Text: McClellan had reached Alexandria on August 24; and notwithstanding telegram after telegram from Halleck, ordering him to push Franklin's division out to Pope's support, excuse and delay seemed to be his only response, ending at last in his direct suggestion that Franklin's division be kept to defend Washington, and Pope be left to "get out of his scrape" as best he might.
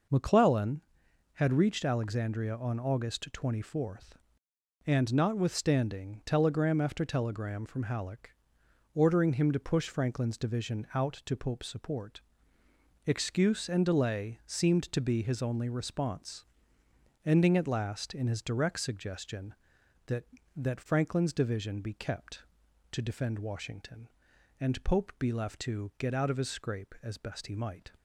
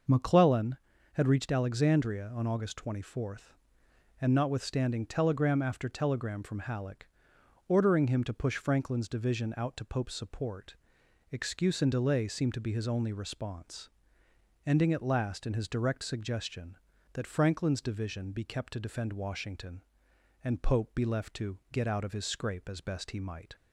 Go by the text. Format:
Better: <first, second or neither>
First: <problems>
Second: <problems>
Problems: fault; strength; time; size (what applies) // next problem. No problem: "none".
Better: second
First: says "that" twice; at 20.5 s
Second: none